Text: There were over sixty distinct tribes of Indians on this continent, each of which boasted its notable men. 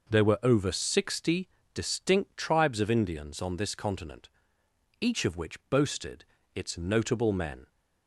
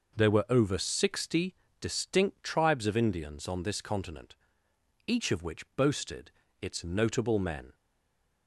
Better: first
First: pauses between "sixty" and "distinct"; slight; at 1.4 s; 0.24 s long // pauses between "boasted" and "its"; slight; at 6.2 s; 0.32 s long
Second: pauses between "sixty" and "distinct"; slight; at 1.5 s; 0.24 s long // pauses between "boasted" and "its"; slight; at 6.3 s; 0.32 s long // stays silent after the last word; slight; from 7.7 s on; 0.7 s long

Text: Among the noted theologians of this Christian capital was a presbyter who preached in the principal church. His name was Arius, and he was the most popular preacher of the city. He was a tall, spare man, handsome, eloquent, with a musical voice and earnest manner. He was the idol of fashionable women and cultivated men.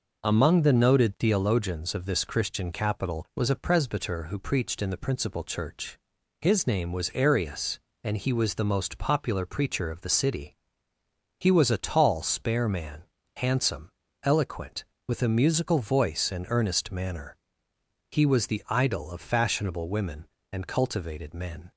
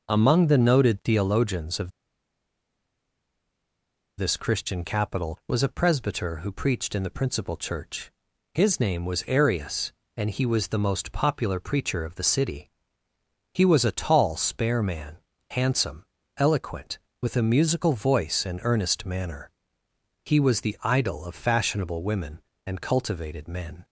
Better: first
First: none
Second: pauses between "of" and "this"; strong; at 1.9 s; 2.2 s long

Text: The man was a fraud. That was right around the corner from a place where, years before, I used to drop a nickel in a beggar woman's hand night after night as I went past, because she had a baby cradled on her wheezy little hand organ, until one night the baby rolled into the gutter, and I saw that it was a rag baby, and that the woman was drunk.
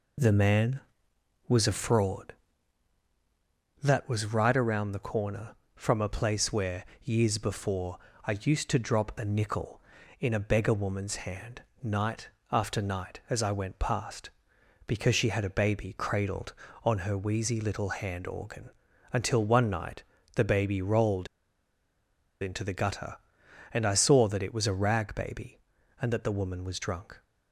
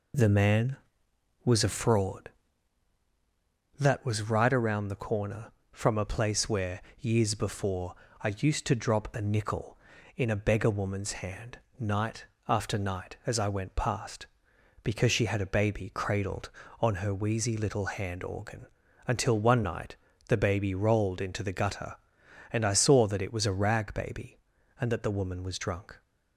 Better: second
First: pauses between "hand" and "night"; slight; at 11.6 s; 0.20 s long // pauses between "night" and "after"; slight; at 12.2 s; 0.24 s long // pauses between "night" and "the"; slight; at 20.0 s; 0.32 s long // pauses between "rolled" and "into"; at 21.2 s; 1.1 s long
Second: pauses between "hand" and "night"; slight; at 11.5 s; 0.20 s long // pauses between "night" and "after"; slight; at 12.2 s; 0.24 s long // pauses between "night" and "the"; slight; at 19.9 s; 0.32 s long

